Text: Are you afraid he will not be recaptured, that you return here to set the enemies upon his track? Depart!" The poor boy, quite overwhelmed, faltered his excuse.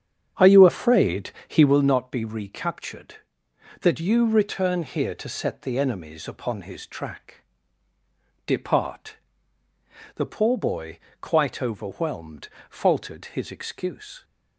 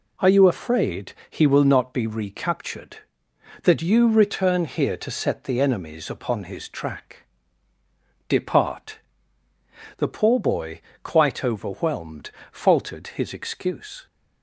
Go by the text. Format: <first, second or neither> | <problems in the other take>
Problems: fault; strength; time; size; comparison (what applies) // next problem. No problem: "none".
second | starts louder than the rest; strong; until 1.7 s; 8 dB // pauses between "afraid" and "he"; slight; at 1.2 s; 0.16 s long; slight in the second